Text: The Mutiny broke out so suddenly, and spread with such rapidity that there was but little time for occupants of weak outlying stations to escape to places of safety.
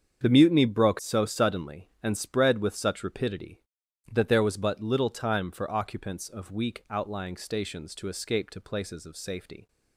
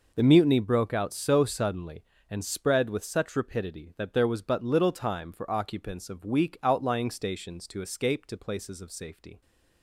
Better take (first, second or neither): second